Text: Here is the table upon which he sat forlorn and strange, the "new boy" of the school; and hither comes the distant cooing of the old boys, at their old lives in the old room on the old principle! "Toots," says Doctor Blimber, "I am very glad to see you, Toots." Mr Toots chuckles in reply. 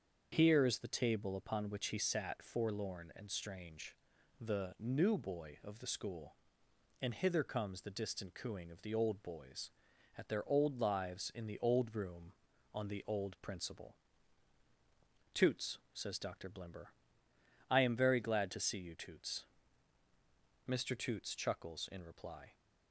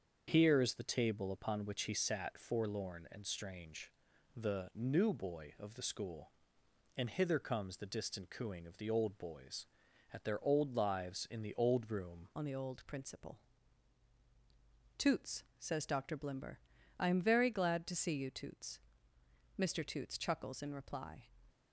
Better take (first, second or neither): first